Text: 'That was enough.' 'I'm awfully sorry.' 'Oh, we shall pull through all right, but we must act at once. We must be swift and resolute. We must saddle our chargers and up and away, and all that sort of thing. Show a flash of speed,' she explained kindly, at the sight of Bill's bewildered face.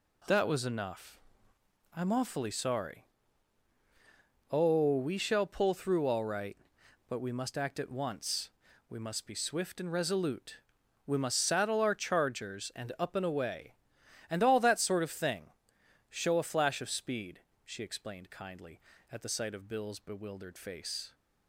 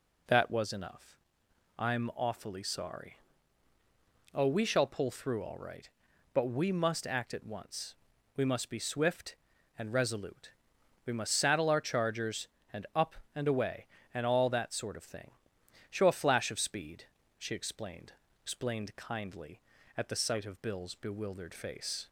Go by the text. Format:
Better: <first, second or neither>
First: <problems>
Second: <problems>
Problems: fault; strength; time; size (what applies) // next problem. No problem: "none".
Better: first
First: none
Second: says "explained" twice; at 18.4 s